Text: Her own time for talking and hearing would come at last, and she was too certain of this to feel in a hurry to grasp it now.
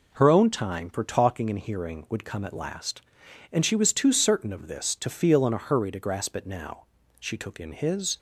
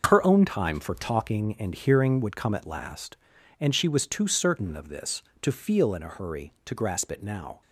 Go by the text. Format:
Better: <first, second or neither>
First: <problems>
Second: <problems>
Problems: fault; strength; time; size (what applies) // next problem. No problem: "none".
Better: second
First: goes on to say "She took in his"; noticeable; from 7.1 s on; 0.98 s long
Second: none